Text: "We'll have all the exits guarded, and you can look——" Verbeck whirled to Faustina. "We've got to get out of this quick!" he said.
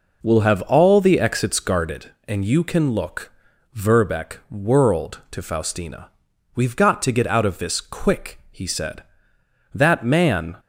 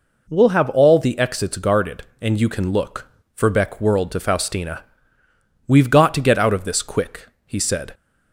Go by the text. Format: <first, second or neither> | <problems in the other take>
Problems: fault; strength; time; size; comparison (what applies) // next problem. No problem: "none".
second | goes on to say "That man"; noticeable; from 9.7 s on; 0.84 s long